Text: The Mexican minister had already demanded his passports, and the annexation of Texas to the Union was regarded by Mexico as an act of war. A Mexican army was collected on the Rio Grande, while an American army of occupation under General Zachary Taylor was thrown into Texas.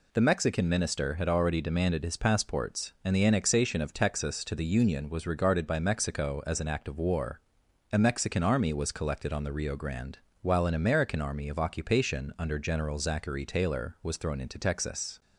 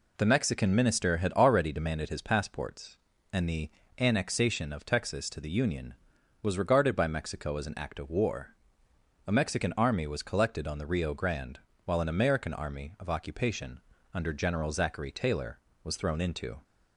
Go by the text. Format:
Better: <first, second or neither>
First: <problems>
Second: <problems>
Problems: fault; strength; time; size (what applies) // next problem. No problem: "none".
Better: first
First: none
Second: pauses between "the" and "annexation"; slight; at 3.6 s; 0.28 s long // pauses between "occupation" and "under"; slight; at 13.7 s; 0.34 s long // stops before "Texas"; at 16.6 s